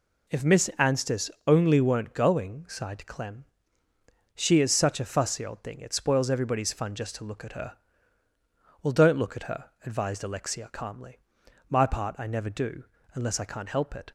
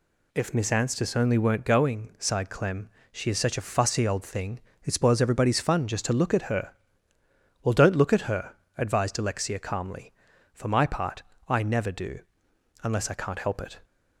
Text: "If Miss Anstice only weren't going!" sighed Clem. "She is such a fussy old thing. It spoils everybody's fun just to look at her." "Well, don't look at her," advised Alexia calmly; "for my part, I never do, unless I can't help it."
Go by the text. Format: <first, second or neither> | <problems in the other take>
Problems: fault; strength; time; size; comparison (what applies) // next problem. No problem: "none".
second | pauses between "Anstice" and "only"; slight; at 1.2 s; 0.18 s long // skips "for"; at 11.4 s